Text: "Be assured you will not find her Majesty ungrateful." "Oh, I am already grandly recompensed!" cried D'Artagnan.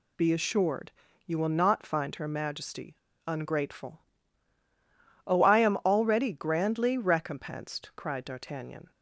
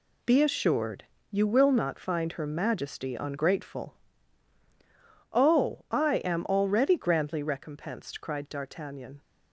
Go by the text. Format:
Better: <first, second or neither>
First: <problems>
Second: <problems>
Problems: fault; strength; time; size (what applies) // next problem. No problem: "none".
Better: second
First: pauses between "assured" and "you"; slight; at 0.9 s; 0.34 s long // pauses between "Majesty" and "ungrateful"; slight; at 2.9 s; 0.28 s long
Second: pauses between "assured" and "you"; slight; at 1.0 s; 0.28 s long